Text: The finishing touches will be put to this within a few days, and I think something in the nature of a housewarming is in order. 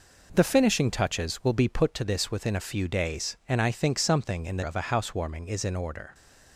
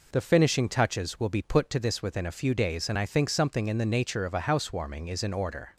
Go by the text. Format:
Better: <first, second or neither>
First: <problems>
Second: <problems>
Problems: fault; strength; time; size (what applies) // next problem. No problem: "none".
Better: second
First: skips "nature"; at 4.6 s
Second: none